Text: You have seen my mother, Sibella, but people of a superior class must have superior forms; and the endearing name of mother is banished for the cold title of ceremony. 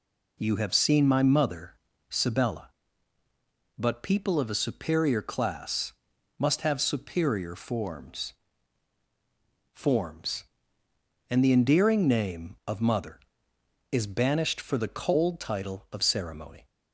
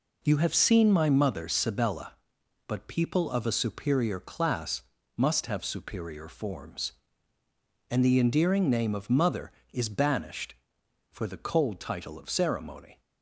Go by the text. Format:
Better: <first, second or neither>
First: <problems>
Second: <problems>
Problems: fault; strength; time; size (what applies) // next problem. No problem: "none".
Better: second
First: pauses between "class" and "must"; noticeable; at 5.9 s; 0.46 s long // says "forms" twice; at 9.7 s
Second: pauses between "class" and "must"; slight; at 4.8 s; 0.36 s long